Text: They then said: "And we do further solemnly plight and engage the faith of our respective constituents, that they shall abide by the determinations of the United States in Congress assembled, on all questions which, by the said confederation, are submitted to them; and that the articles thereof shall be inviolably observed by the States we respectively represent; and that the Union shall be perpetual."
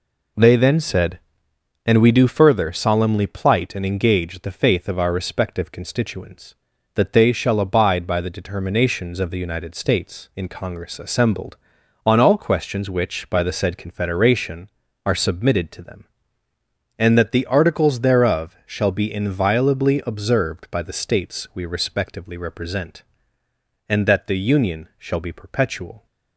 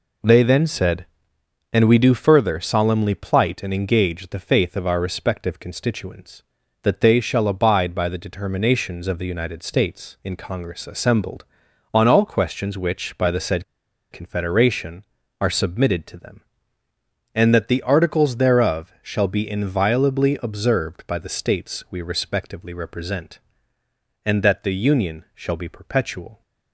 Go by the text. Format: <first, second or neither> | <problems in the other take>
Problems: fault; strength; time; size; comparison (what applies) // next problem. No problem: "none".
first | pauses between "said" and "confederation"; noticeable; at 13.6 s; 0.47 s long